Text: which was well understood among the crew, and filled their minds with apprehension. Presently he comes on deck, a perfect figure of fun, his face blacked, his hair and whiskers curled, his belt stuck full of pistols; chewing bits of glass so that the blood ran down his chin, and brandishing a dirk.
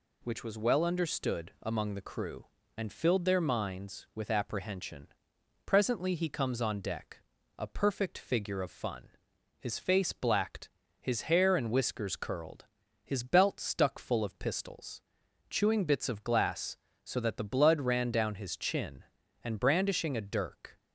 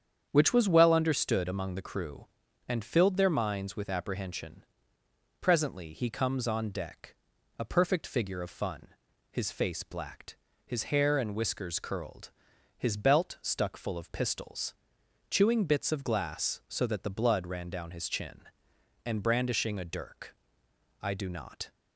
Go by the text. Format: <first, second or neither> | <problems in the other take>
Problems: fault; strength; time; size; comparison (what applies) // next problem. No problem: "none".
first | starts louder than the rest; strong; until 1.3 s; 8 dB // goes on to say "I do not"; noticeable; from 21.0 s on; 0.68 s long